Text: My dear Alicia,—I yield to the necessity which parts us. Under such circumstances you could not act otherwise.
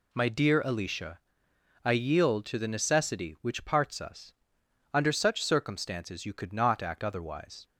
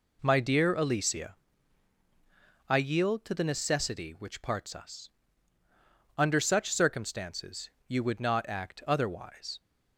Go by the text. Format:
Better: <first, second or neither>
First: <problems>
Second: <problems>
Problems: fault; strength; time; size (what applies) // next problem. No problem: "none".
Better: first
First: none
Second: pauses between "circumstances" and "you"; slight; at 7.7 s; 0.18 s long // says "would" for "could"; at 8.0 s